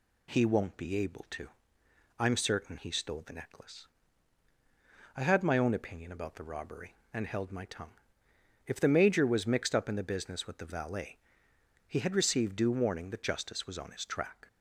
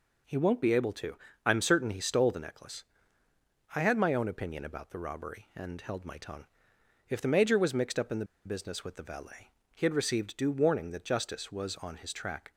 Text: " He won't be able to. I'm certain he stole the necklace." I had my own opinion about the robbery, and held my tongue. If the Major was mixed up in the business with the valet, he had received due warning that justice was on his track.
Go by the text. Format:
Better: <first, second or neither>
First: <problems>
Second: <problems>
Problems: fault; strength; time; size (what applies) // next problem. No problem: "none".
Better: first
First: none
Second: pauses between "the" and "business"; slight; at 8.2 s; 0.20 s long